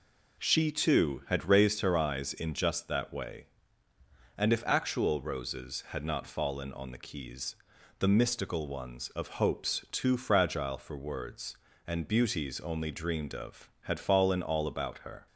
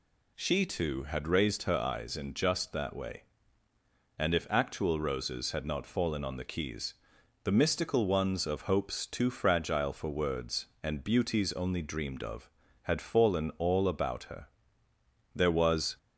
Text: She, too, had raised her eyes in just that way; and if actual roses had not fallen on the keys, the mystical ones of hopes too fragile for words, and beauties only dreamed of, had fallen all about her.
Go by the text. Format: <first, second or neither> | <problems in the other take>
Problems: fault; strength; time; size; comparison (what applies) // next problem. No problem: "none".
first | goes on to say "There was"; noticeable; from 15.3 s on; 0.62 s long